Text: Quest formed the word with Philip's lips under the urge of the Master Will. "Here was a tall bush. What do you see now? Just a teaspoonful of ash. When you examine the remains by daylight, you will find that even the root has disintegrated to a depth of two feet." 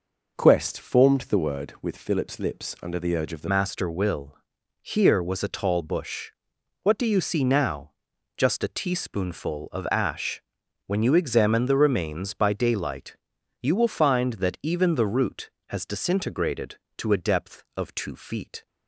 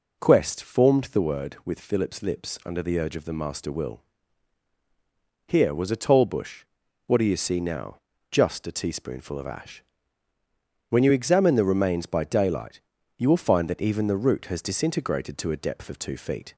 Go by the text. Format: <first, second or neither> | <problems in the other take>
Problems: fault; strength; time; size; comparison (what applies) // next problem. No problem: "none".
second | changes voice at "Master"; from 3.4 s on; 15.2 s long